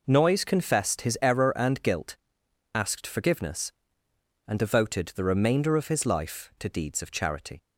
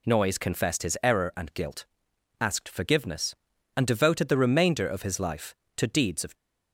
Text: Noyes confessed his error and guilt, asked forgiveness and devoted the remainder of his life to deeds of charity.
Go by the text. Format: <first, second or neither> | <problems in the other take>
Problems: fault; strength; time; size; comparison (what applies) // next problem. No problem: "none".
first | stops before "charity"; at 6.3 s